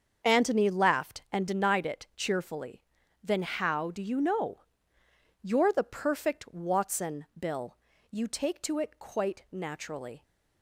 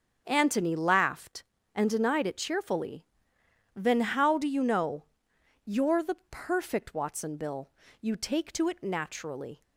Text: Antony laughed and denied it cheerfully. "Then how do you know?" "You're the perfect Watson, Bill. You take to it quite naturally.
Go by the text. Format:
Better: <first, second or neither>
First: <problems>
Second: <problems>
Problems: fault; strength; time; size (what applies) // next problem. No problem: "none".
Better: first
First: starts louder than the rest; until 1.3 s; 7 dB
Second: starts louder than the rest; until 1.2 s; 7 dB // skips "quite"; at 8.8 s